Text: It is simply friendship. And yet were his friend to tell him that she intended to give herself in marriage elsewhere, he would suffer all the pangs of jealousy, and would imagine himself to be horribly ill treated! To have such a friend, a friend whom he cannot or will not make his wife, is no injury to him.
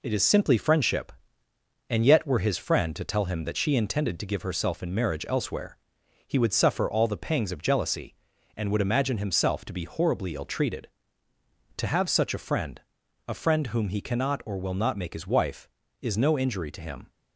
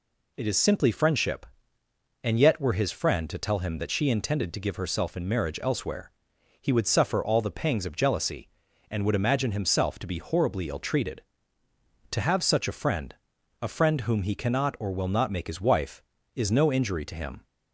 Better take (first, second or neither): second